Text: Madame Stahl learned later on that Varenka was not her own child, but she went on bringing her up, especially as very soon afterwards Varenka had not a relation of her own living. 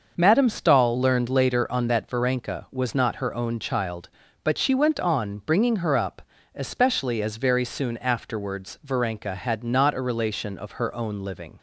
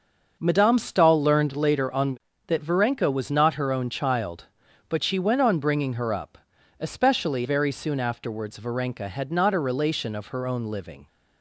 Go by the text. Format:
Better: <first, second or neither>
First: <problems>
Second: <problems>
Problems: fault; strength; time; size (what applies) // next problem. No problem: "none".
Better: first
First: starts louder than the rest; until 1.1 s; 6 dB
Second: starts louder than the rest; noticeable; until 1.4 s; 6 dB // skips "as"; at 7.4 s